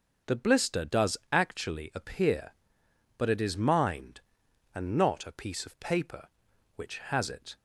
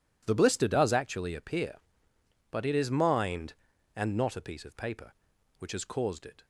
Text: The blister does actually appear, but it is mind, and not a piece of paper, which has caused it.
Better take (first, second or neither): second